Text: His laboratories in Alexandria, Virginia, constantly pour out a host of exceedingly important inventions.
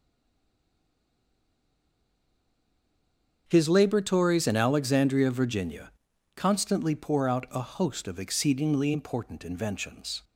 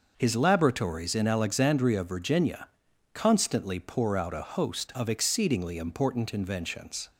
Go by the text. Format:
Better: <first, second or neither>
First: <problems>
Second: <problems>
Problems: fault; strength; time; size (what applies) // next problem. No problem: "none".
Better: second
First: stays silent before the first word; strong; until 3.4 s; 3.4 s long // starts louder than the rest; until 4.4 s; 6.5 dB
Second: none